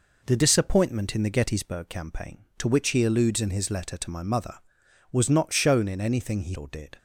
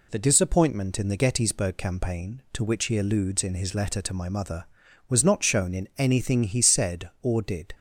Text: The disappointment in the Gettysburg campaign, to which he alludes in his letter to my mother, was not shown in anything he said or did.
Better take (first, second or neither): second